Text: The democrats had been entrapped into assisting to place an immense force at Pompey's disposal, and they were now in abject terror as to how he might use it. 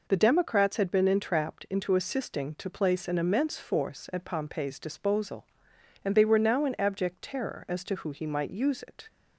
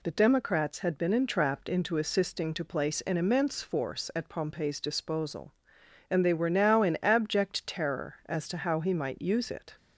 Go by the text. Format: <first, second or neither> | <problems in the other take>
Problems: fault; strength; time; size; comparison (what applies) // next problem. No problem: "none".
second | says "who" for "how"; at 7.9 s